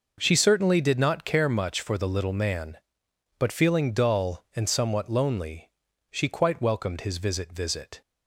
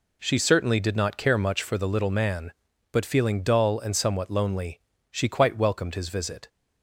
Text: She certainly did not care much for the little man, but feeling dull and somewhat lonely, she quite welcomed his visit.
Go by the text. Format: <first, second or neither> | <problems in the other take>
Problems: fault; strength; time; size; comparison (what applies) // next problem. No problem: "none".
second | says "visit" twice; at 7.5 s